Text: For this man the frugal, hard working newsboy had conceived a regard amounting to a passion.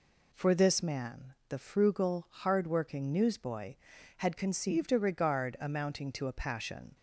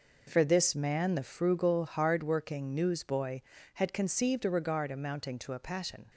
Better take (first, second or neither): neither